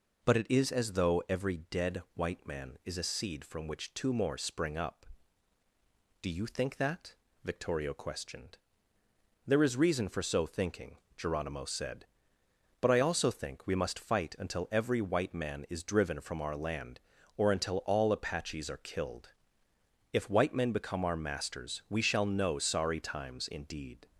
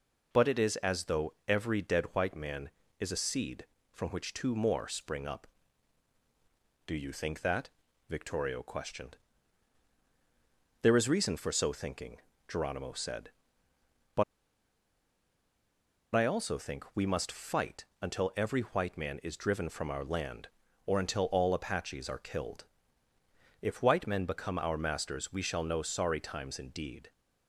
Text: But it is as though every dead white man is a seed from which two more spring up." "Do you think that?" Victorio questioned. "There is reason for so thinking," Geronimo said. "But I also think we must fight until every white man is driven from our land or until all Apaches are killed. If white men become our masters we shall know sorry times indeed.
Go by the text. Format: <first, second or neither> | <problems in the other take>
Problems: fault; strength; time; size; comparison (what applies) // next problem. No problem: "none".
first | pauses between "But" and "I"; strong; at 14.2 s; 1.9 s long // pauses between "fight" and "until"; slight; at 17.8 s; 0.16 s long